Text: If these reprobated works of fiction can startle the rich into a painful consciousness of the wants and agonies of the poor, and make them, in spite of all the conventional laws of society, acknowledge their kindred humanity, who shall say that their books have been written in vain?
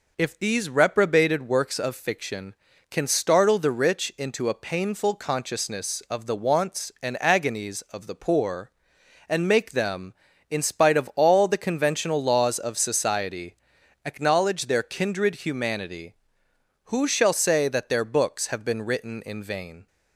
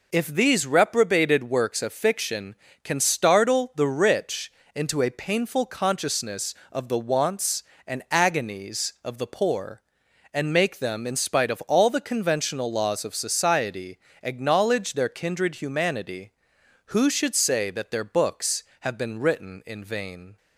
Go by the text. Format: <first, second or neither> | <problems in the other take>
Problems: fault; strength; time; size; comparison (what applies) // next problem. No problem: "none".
first | pauses between "rich" and "into"; slight; at 4.5 s; 0.20 s long // says "should" for "shall"; at 17.1 s